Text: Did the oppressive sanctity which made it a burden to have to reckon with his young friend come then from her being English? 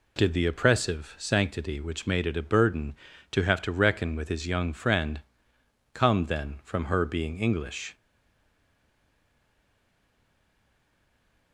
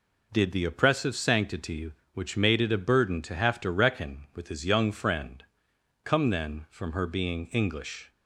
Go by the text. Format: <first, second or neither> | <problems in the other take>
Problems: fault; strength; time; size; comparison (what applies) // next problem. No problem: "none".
second | pauses between "friend" and "come"; noticeable; at 5.2 s; 0.72 s long; noticeable in the second // stays silent after the last word; strong; from 7.9 s on; 3.6 s long